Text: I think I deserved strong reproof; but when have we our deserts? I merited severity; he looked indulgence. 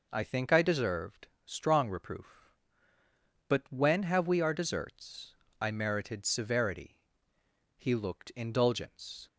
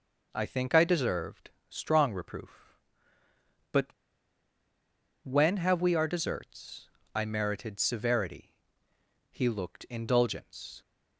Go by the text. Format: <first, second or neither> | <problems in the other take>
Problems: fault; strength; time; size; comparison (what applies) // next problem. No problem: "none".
first | pauses between "deserved" and "strong"; slight; at 1.5 s; 0.18 s long; slight in the first // pauses between "but" and "when"; strong; at 3.8 s; 1.3 s long